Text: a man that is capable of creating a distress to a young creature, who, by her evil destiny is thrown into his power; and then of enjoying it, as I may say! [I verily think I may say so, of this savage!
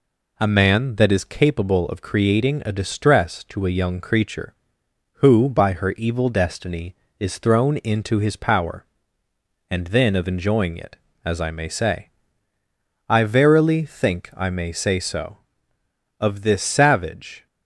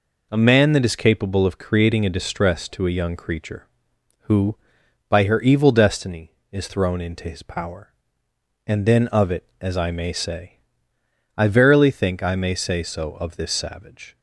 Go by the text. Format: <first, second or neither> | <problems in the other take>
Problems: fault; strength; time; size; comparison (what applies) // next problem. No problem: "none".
first | skips "enjoying"; at 9.3 s